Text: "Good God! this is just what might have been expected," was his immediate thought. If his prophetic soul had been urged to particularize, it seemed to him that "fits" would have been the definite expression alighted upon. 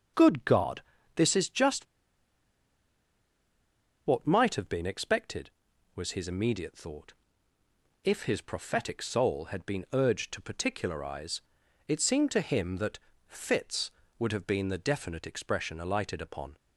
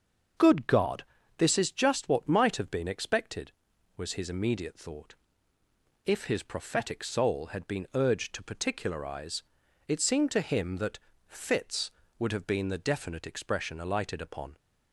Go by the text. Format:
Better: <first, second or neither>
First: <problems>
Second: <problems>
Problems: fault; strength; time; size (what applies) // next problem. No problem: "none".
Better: second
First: starts louder than the rest; until 1.4 s; 6.5 dB // pauses between "just" and "what"; strong; at 1.8 s; 2.2 s long // pauses between "that" and "fits"; slight; at 12.9 s; 0.30 s long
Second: starts louder than the rest; until 1.7 s; 6.5 dB // pauses between "that" and "fits"; slight; at 10.9 s; 0.30 s long